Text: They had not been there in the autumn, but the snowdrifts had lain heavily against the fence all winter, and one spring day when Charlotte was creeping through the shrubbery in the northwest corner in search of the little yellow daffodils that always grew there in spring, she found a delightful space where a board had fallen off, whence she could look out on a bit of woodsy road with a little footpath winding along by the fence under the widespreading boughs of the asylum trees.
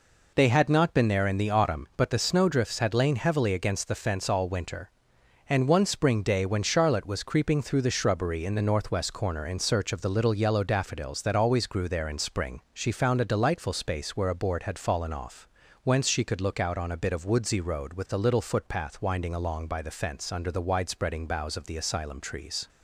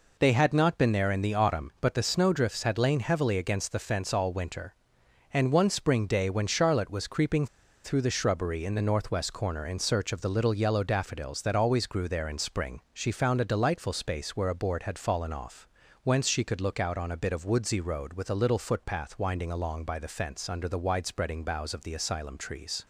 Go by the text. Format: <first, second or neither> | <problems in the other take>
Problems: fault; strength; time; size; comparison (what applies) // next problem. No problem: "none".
first | pauses between "creeping" and "through"; at 7.4 s; 0.38 s long